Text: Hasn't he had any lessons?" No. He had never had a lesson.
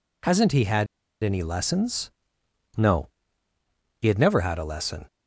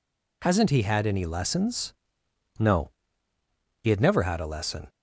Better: second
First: pauses between "had" and "any"; at 0.8 s; 0.37 s long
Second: none

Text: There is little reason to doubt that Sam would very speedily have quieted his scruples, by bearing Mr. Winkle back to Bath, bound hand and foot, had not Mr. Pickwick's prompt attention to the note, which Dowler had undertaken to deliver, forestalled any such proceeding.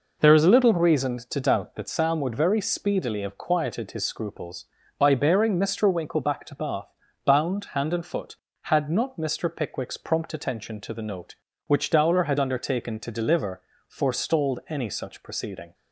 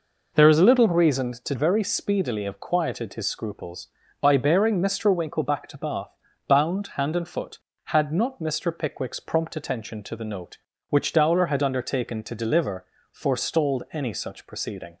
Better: first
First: none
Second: skips "doubt that Sam would"; at 1.5 s

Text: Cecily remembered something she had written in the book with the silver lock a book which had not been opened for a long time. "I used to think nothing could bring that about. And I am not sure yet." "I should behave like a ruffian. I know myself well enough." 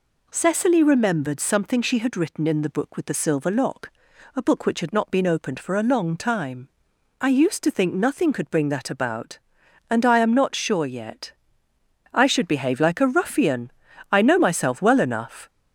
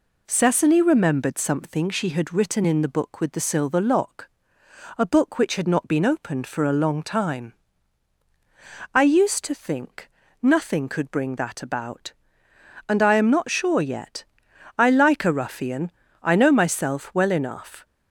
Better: first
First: pauses between "lock" and "a"; noticeable; at 3.8 s; 0.46 s long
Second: pauses between "lock" and "a"; noticeable; at 4.2 s; 0.68 s long // pauses between "think" and "nothing"; slight; at 10.0 s; 0.32 s long // skips "should behave"; at 14.9 s

